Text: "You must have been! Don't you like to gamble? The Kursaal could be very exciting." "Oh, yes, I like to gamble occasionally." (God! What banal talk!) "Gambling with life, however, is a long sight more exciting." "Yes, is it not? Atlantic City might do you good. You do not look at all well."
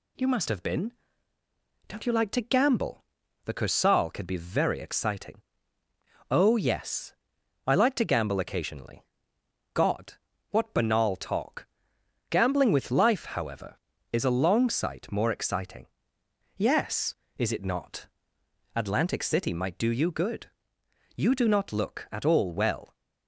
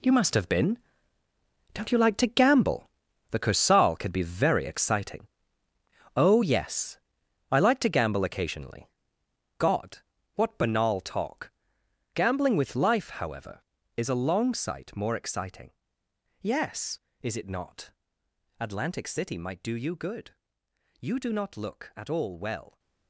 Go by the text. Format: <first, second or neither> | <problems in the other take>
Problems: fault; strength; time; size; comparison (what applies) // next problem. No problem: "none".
first | gets quieter; strong; throughout; 11 dB